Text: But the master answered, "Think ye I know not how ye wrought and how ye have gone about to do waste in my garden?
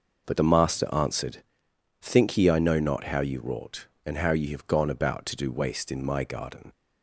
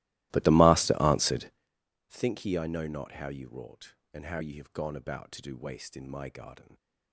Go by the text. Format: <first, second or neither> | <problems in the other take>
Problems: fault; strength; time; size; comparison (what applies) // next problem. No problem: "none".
first | starts louder than the rest; strong; until 1.7 s; 17.5 dB